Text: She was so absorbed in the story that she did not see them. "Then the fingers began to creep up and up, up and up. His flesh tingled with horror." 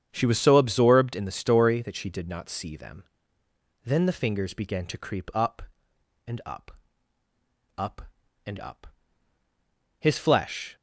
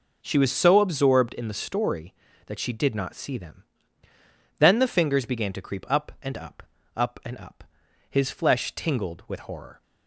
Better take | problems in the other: second | starts louder than the rest; strong; until 1.1 s; 8 dB // stops before "tingled with horror"; at 10.7 s

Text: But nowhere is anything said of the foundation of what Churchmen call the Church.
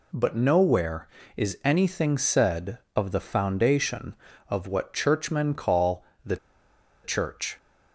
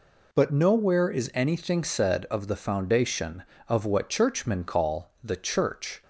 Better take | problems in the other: second | pauses between "call" and "the"; slight; at 6.0 s; 0.20 s long // pauses between "the" and "Church"; noticeable; at 6.3 s; 0.67 s long

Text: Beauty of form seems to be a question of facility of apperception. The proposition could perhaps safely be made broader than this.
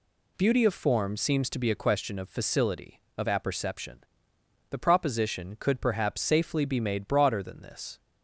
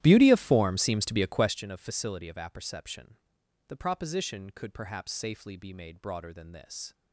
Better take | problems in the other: first | starts louder than the rest; strong; until 1.6 s; 13.5 dB

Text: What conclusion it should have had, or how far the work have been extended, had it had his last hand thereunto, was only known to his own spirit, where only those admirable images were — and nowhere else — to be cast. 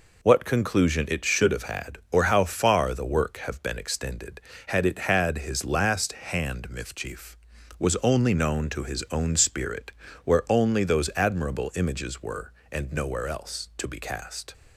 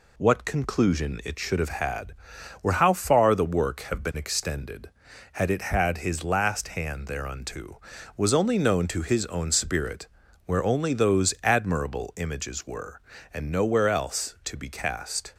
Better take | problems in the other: second | says "mifchief" for "thereunto"; at 6.7 s

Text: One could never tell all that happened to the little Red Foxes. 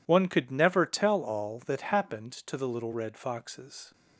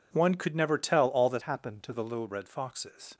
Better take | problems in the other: first | changes voice from "happened" to "to"; from 1.4 to 1.9 s; 0.5 s long

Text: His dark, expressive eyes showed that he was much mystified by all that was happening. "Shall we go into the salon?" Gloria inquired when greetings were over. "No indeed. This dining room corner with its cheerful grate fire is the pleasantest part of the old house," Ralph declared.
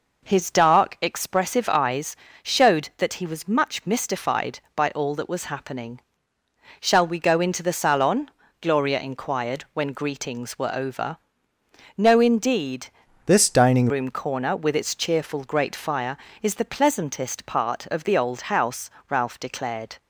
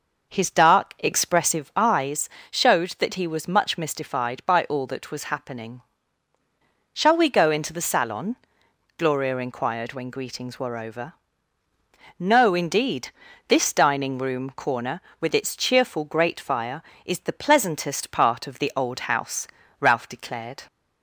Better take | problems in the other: second | pauses between "eyes" and "showed"; slight; at 2.1 s; 0.28 s long; slight in the second // changes voice from "This" to "dining"; from 13.2 to 13.8 s; 0.6 s long

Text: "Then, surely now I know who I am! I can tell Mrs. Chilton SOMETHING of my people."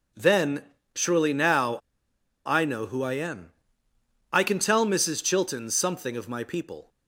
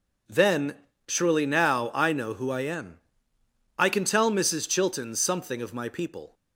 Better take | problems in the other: second | pauses between "now" and "I"; noticeable; at 1.7 s; 0.67 s long

